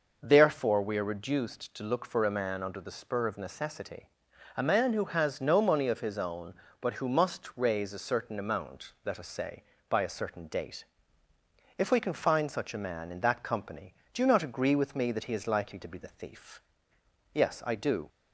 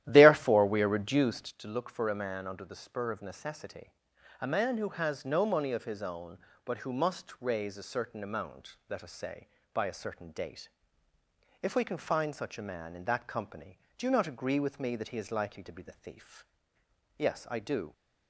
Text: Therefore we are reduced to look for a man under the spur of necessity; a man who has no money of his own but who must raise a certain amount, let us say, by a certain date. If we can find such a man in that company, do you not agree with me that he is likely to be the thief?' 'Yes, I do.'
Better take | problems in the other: first | starts louder than the rest; strong; until 1.5 s; 12.5 dB

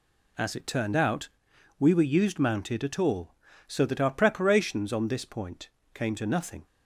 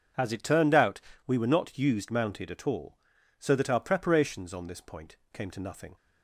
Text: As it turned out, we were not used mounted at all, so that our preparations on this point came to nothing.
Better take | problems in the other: second | skips "not"; at 2.0 s // pauses between "point" and "came"; slight; at 5.7 s; 0.22 s long; slight in the second

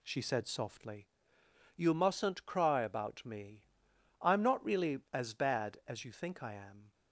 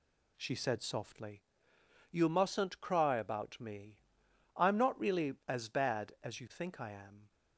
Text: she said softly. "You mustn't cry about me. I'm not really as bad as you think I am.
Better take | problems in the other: neither | none

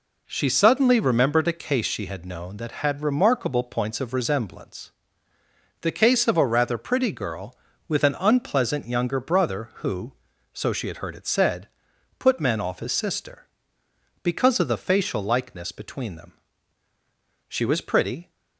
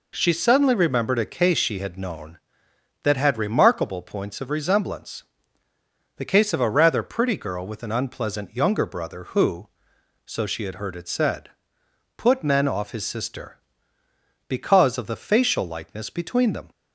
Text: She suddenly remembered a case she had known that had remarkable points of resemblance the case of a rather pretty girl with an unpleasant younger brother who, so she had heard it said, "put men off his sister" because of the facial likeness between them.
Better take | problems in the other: second | pauses between "resemblance" and "the"; noticeable; at 4.9 s; 0.92 s long; noticeable in the second // goes on to say "She was pretty"; noticeable; from 17.4 s on; 0.82 s long

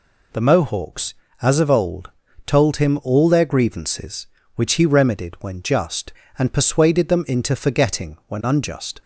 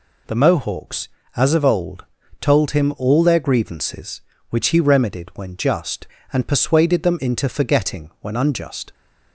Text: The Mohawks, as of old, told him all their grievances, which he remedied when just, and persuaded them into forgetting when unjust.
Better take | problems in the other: neither | none

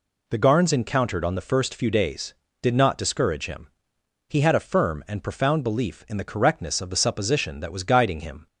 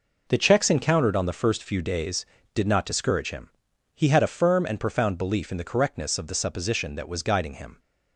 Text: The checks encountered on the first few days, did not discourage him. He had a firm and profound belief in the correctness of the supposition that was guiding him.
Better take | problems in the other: second | says "garns" for "checks"; at 0.3 s

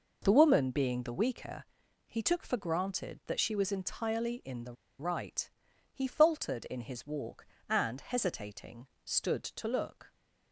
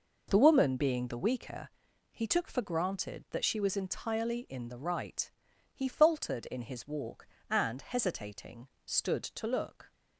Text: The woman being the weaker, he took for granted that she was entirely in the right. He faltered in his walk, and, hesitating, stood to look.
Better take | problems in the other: second | pauses between "the" and "right"; slight; at 4.7 s; 0.26 s long

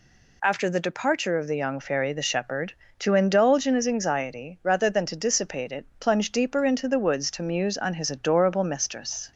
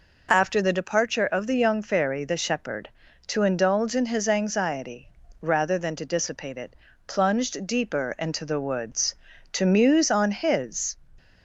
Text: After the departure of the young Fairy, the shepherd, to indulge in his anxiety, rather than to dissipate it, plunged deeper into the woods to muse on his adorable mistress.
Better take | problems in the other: first | stops before "adorable mistress"; at 11.1 s

